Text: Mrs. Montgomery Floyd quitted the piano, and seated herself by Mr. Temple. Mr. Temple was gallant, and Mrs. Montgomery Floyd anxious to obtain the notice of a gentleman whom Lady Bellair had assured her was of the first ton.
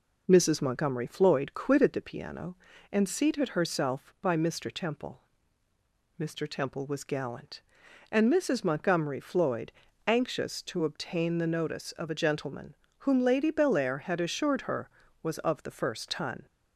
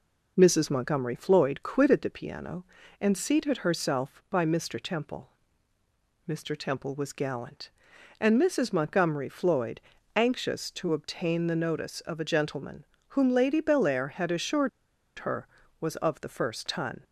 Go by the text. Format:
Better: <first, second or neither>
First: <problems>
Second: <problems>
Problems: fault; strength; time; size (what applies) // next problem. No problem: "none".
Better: first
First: pauses between "Floyd" and "anxious"; at 9.6 s; 0.38 s long // pauses between "gentleman" and "whom"; slight; at 12.7 s; 0.24 s long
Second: pauses between "Floyd" and "anxious"; at 9.7 s; 0.38 s long // pauses between "gentleman" and "whom"; slight; at 12.8 s; 0.24 s long // pauses between "assured" and "her"; noticeable; at 14.6 s; 0.49 s long